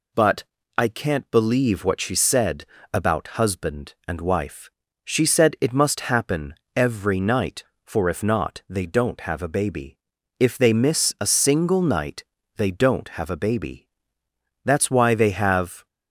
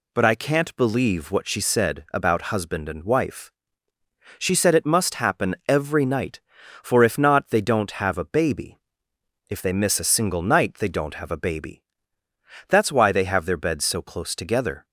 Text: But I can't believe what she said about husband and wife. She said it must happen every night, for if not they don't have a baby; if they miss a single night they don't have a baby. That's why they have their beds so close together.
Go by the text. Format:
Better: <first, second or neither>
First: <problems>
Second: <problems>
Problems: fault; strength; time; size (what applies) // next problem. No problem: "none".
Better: second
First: pauses between "But" and "I"; slight; at 0.4 s; 0.32 s long // pauses between "said" and "about"; slight; at 2.6 s; 0.28 s long // pauses between "happen" and "every"; slight; at 6.5 s; 0.20 s long // pauses between "night" and "they"; slight; at 12.2 s; 0.32 s long // stops before "their beds so close together"; at 15.8 s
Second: none